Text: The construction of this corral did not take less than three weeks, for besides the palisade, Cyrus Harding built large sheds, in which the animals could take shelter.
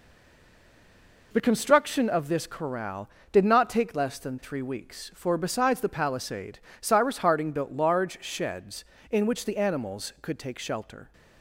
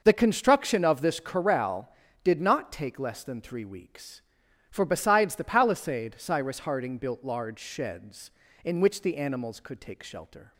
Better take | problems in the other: second | stays silent before the first word; noticeable; until 1.3 s; 1.3 s long

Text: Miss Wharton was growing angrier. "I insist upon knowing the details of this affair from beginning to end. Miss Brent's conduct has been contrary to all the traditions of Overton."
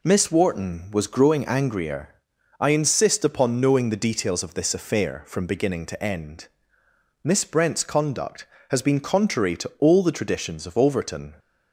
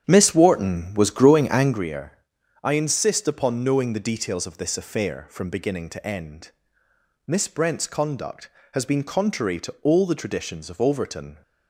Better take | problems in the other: first | starts louder than the rest; strong; until 1.9 s; 9 dB

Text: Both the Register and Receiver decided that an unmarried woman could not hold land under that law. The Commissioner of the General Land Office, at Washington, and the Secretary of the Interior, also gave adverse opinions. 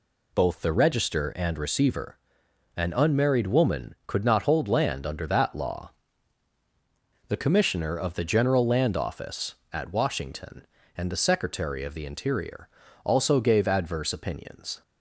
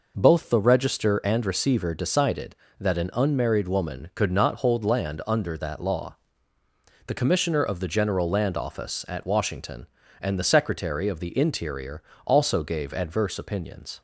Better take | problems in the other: second | skips "decided that"; at 2.4 s

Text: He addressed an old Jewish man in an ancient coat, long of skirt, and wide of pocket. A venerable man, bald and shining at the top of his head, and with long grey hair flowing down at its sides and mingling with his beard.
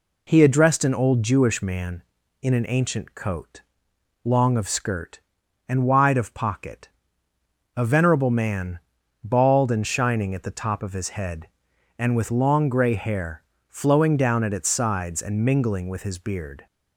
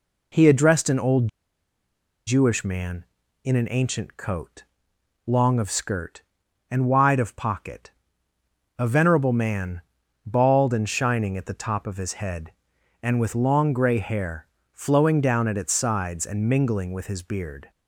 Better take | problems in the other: first | pauses between "old" and "Jewish"; at 1.2 s; 0.99 s long // pauses between "hair" and "flowing"; slight; at 14.4 s; 0.24 s long; slight in the first

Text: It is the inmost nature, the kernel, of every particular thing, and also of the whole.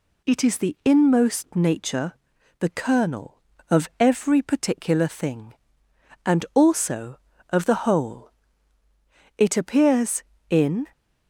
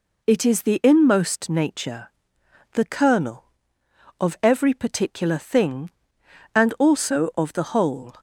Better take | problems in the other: second | goes on to say "It appears in"; from 9.3 s on; 1.5 s long

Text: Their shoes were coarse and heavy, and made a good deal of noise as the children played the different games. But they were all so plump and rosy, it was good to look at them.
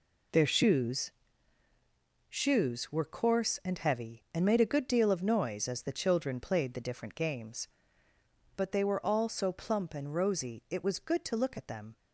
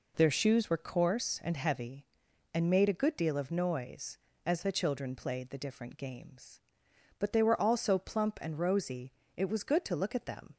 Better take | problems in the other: second | says "shoes" twice; at 2.2 s

